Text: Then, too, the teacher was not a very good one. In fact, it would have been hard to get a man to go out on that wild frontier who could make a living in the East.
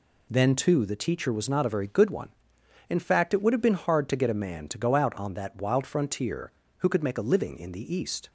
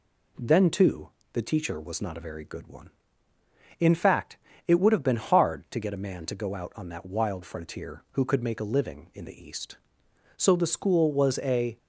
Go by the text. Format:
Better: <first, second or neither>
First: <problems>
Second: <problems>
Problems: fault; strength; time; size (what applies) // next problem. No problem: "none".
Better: first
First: none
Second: goes on to say "So the school was a"; from 10.3 s on; 1.4 s long